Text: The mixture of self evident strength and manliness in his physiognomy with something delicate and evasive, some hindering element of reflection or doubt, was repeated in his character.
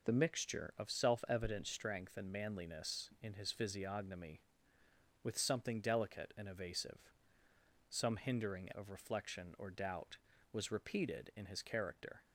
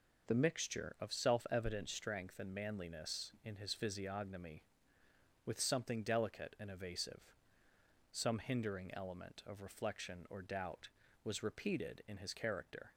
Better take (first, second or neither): second